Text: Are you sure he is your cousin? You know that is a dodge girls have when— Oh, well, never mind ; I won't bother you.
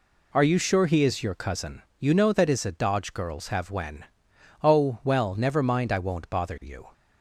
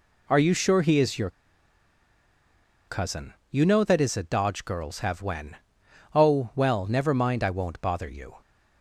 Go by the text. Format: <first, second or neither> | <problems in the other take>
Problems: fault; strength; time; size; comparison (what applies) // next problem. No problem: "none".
first | pauses between "your" and "cousin"; strong; at 1.2 s; 1.5 s long